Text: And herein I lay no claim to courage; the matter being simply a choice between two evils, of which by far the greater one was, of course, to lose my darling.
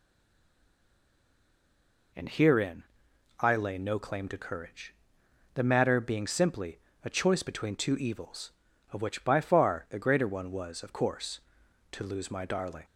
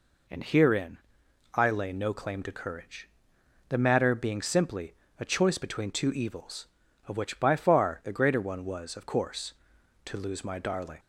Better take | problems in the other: second | stays silent before the first word; until 2.1 s; 2.1 s long // pauses between "herein" and "I"; noticeable; at 2.8 s; 0.58 s long; noticeable in the second // pauses between "simply" and "a"; slight; at 6.7 s; 0.26 s long; slight in the second

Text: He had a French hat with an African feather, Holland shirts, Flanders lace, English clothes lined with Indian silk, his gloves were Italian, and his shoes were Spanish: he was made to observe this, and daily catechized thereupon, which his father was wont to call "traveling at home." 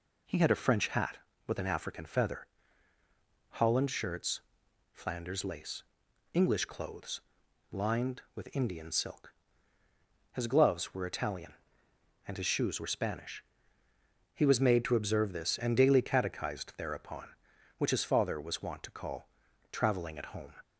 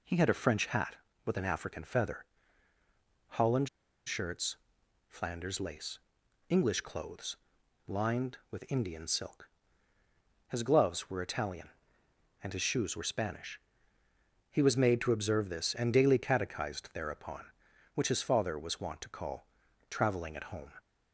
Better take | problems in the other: first | pauses between "Holland" and "shirts"; at 3.6 s; 0.39 s long // pauses between "clothes" and "lined"; noticeable; at 7.3 s; 0.50 s long; noticeable in the first // pauses between "call" and "traveling"; at 19.4 s; 0.42 s long; also in the first

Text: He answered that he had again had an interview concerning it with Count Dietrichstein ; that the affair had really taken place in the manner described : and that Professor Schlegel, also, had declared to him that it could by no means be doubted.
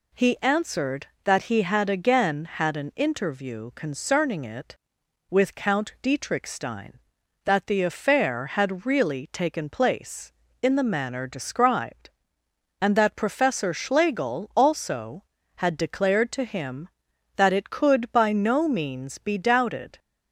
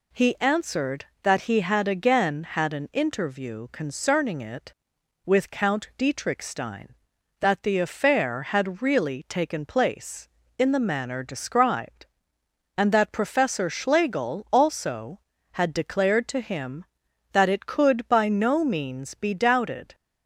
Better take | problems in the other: neither | none

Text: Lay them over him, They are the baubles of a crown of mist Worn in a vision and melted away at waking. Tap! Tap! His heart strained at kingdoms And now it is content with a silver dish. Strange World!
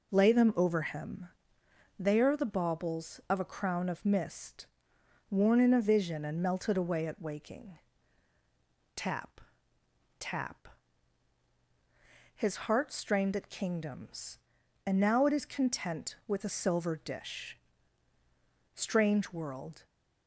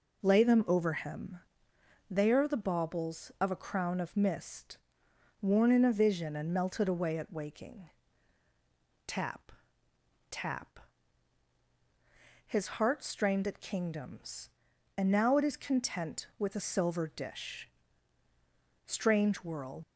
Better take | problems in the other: first | pauses between "mist" and "Worn"; noticeable; at 4.7 s; 0.62 s long; noticeable in the first // leaves "World" unfinished; at 19.8 s; 145 ms

